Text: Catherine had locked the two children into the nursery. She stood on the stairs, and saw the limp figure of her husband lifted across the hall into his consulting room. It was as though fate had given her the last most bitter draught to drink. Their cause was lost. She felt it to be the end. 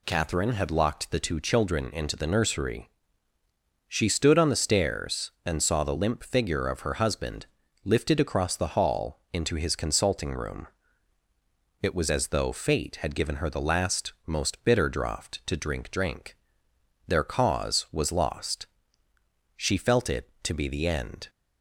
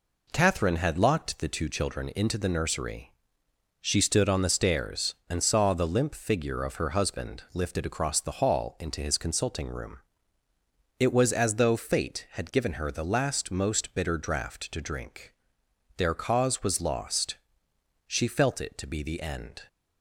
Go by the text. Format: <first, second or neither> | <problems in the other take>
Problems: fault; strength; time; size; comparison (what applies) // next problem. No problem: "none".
second | pauses between "husband" and "lifted"; at 7.4 s; 0.38 s long // says "drink" twice; at 15.9 s